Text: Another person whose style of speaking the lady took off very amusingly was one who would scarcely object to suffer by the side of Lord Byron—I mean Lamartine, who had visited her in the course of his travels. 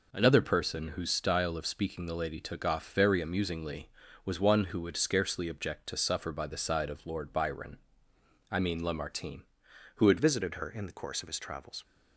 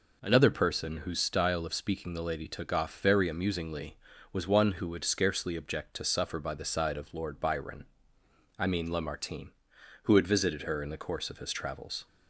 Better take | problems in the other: second | changes voice at "visited"; from 10.1 s on; 1.7 s long

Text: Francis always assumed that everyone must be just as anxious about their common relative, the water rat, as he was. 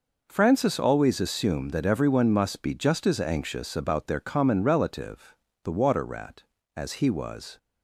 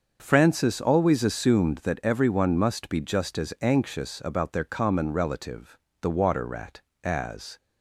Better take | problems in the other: first | starts louder than the rest; until 1.2 s; 6.5 dB // stops before "he was"; at 7.5 s

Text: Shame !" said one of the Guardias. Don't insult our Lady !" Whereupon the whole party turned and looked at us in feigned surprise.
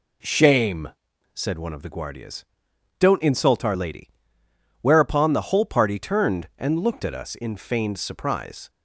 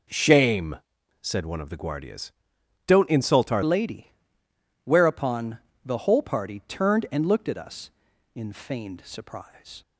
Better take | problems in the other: first | changes voice at "Lady"; from 3.6 s on; 6.2 s long // pauses between "Whereupon" and "the"; slight; at 5.5 s; 0.26 s long

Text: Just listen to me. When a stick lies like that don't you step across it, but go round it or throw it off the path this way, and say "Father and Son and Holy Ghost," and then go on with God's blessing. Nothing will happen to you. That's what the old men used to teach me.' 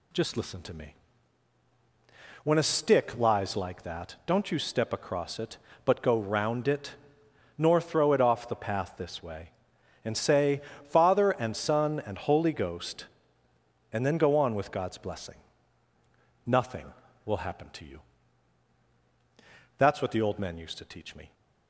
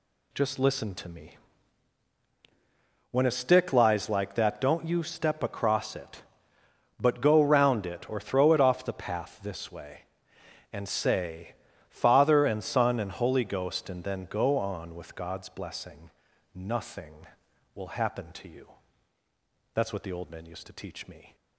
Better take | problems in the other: second | says "nor" for "or"; at 7.5 s // pauses between "say" and "Father"; slight; at 10.6 s; 0.28 s long; slight in the second

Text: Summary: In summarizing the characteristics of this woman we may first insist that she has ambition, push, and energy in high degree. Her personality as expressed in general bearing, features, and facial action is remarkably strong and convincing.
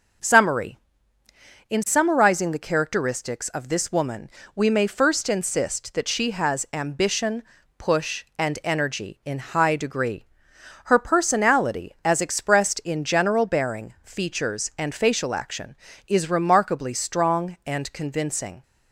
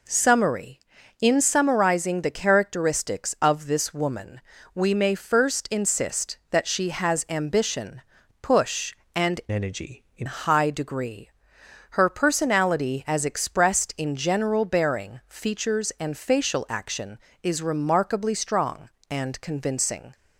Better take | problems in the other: first | pauses between "woman" and "we"; slight; at 4.4 s; 0.32 s long; slight in the first // changes voice from "energy" to "in"; from 9.5 to 10.2 s; 0.7 s long

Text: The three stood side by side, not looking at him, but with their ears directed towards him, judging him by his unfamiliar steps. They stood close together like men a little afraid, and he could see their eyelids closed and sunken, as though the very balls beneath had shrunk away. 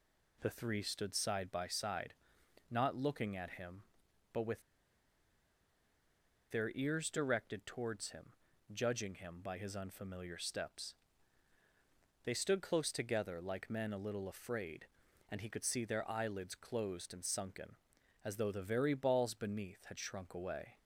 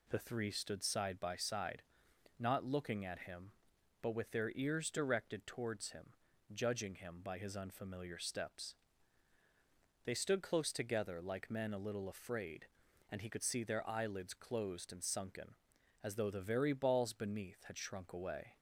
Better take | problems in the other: second | pauses between "with" and "their"; strong; at 4.6 s; 1.8 s long

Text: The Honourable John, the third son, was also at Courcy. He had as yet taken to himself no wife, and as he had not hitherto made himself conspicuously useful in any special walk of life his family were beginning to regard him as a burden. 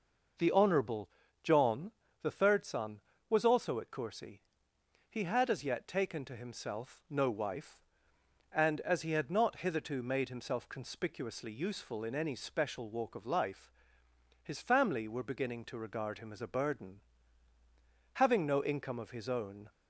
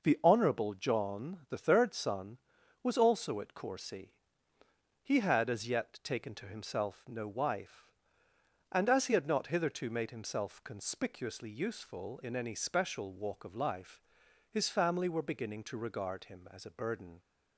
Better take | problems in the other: second | pauses between "Honourable" and "John"; slight; at 1.0 s; 0.34 s long // pauses between "life" and "his"; noticeable; at 13.6 s; 0.72 s long; noticeable in the second // goes on to say "Having no income of his own"; from 18.1 s on; 1.5 s long

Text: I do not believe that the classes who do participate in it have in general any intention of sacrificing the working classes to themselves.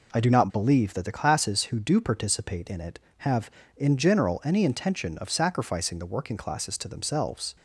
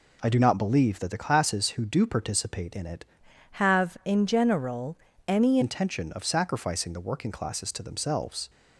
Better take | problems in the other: first | changes voice from "have" to "any"; from 3.5 to 5.6 s; 2.1 s long // pauses between "general" and "any"; slight; at 4.9 s; 0.32 s long

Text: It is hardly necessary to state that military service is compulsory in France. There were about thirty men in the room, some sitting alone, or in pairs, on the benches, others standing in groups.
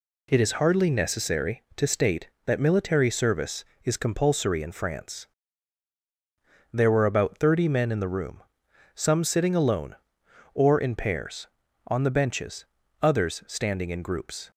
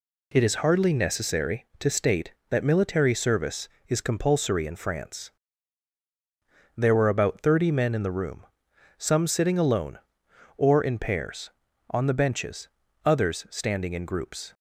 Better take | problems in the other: neither | none

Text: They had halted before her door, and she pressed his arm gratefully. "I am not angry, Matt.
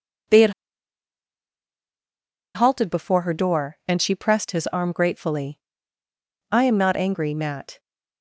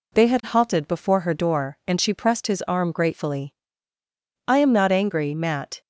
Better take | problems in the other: second | pauses between "had" and "halted"; strong; at 0.5 s; 2.0 s long

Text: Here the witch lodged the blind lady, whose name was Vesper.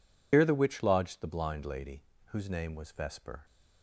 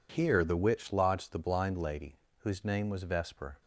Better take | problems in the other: second | loses the start of "Here"; at 0.3 s; 90 ms

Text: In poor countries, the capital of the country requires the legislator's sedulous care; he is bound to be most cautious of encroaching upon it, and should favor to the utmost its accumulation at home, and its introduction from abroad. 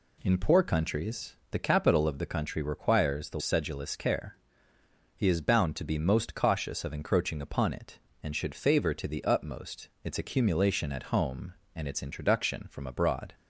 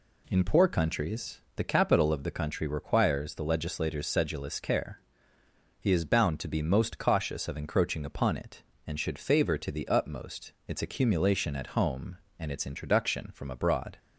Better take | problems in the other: second | skips "legislator's"; at 3.4 s

